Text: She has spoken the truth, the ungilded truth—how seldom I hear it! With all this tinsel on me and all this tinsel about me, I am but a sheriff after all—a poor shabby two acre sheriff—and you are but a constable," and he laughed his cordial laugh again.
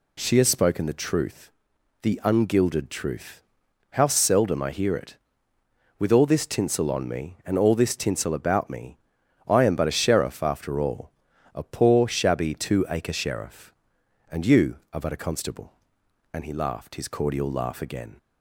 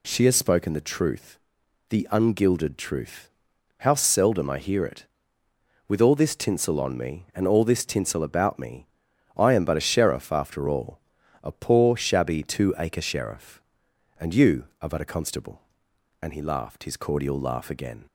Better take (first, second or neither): neither